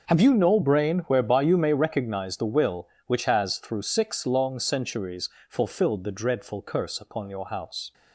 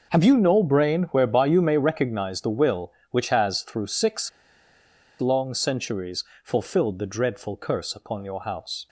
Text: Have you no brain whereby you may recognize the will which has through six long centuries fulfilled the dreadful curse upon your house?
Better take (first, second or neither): first